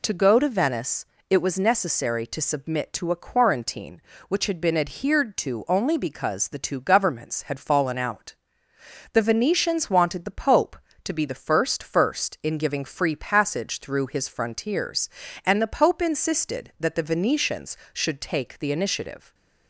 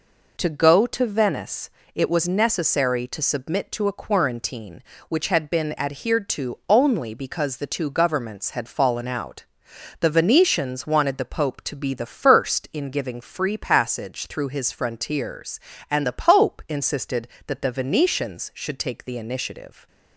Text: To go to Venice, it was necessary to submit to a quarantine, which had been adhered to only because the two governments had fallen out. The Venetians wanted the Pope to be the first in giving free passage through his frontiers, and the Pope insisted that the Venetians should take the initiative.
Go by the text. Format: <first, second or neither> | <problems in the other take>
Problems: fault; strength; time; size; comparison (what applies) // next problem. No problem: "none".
second | says "first" twice; at 11.8 s